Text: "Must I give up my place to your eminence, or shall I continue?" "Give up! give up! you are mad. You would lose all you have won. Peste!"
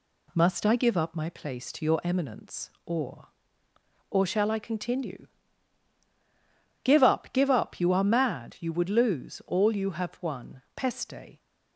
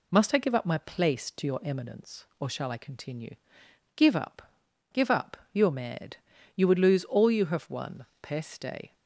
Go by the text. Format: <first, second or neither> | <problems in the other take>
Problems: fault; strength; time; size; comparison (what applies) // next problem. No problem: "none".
second | says "or" twice; at 4.1 s